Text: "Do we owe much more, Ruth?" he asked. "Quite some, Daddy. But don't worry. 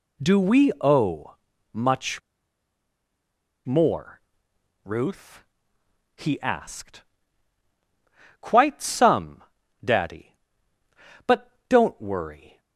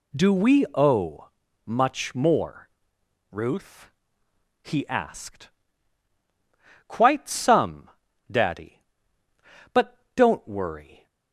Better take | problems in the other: second | pauses between "owe" and "much"; slight; at 1.3 s; 0.36 s long; slight in the second // pauses between "much" and "more"; strong; at 2.2 s; 1.4 s long // pauses between "But" and "don't"; slight; at 11.4 s; 0.20 s long; slight in the second

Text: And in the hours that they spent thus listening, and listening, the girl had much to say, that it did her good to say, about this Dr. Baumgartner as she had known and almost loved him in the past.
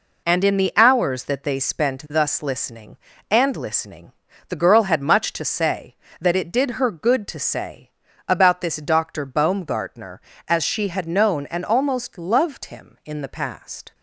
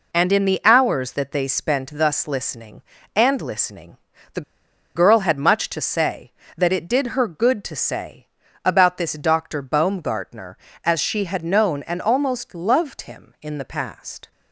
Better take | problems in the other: first | pauses between "the" and "girl"; noticeable; at 4.4 s; 0.54 s long

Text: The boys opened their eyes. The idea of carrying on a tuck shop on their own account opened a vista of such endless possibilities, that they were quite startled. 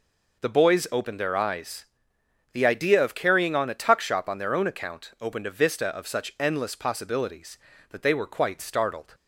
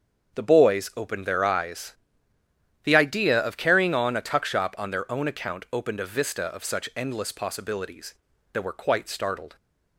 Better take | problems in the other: first | starts louder than the rest; strong; until 1.4 s; 7 dB // skips "they"; at 8.6 s

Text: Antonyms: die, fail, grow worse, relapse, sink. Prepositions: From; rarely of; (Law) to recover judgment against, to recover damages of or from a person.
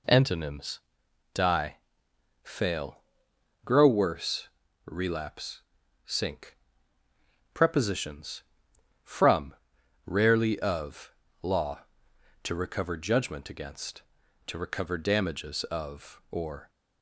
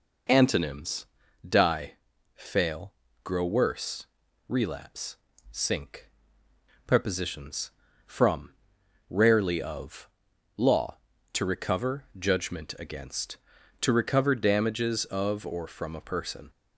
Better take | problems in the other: second | stops before "from a person"; at 16.6 s

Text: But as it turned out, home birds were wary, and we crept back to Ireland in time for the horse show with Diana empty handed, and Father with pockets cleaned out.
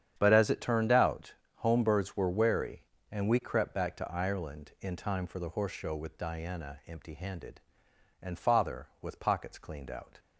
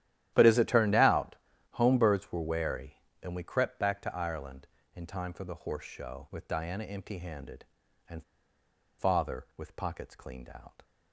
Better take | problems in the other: first | starts louder than the rest; strong; until 1.3 s; 12 dB; strong in the first // pauses between "and" and "Father"; noticeable; at 8.2 s; 0.75 s long

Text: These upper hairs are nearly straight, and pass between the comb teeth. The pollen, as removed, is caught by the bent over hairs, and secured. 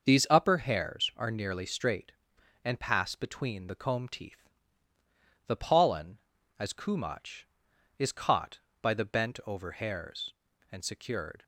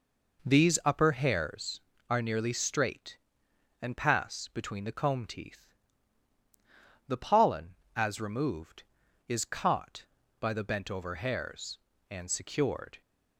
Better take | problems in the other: second | starts louder than the rest; noticeable; until 1.1 s; 6 dB // says "kumach" for "removed"; at 6.7 s

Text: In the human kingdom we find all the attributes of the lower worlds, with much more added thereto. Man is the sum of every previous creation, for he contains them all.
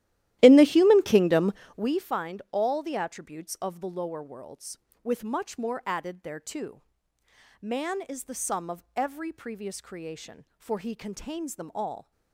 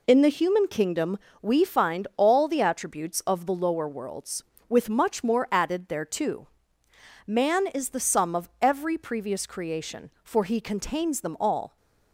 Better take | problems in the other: second | starts louder than the rest; strong; until 1.9 s; 14.5 dB // pauses between "kingdom" and "we"; slight; at 1.5 s; 0.22 s long; slight in the second

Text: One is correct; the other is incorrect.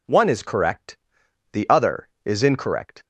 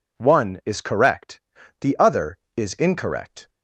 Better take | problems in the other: neither | none

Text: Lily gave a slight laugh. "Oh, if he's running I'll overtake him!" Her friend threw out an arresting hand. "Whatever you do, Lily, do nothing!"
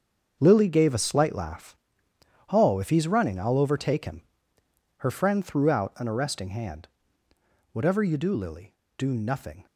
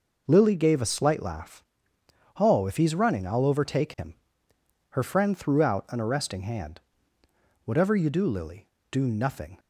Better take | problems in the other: second | gets quieter; strong; throughout; 12.5 dB

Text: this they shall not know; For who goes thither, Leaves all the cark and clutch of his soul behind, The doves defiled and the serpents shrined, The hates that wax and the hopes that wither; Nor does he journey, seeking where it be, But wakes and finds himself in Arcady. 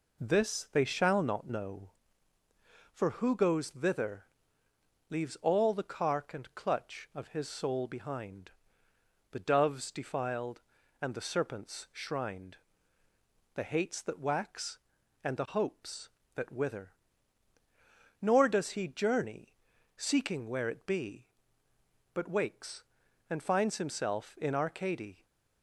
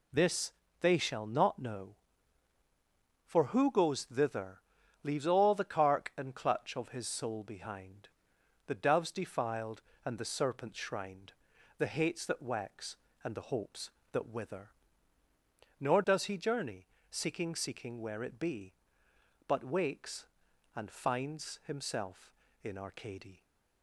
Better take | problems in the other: first | pauses between "this" and "they"; slight; at 0.5 s; 0.30 s long // says "seeking" twice; at 17.5 s

